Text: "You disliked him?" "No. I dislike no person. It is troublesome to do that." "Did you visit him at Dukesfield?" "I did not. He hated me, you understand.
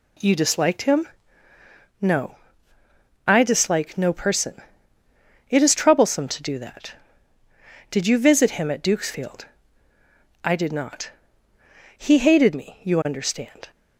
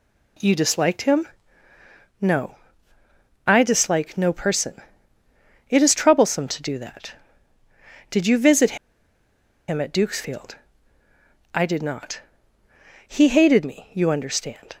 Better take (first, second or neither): first